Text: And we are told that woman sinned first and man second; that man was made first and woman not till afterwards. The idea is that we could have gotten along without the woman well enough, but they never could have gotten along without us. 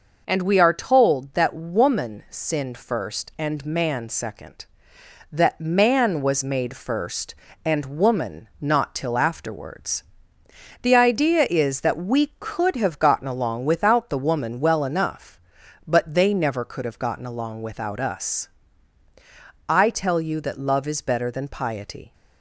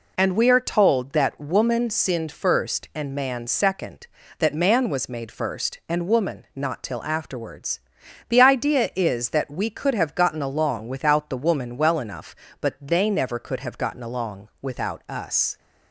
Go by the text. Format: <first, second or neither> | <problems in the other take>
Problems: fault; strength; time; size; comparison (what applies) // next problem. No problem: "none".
second | goes on to say "I tell you that love is better than piety"; strong; from 19.6 s on; 2.4 s long